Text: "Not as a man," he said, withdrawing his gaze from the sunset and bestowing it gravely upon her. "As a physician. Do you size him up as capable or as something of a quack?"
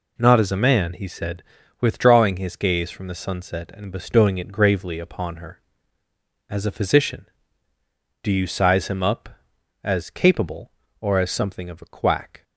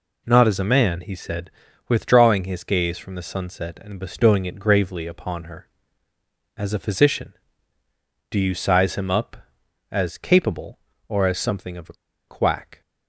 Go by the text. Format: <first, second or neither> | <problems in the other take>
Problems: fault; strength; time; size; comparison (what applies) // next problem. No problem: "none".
first | pauses between "a" and "quack"; slight; at 11.9 s; 0.34 s long